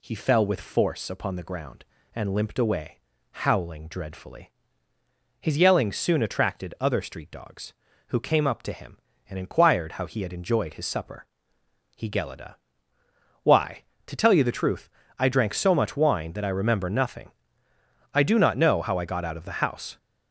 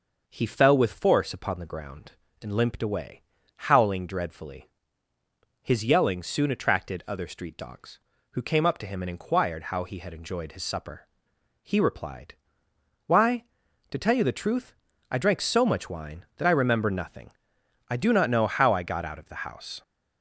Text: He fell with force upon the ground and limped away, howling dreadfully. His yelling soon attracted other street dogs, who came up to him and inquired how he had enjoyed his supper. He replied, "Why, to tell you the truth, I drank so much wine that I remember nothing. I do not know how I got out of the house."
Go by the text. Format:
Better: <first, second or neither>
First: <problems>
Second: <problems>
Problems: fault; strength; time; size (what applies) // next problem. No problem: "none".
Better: second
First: says "gelida" for "replied"; at 12.0 s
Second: none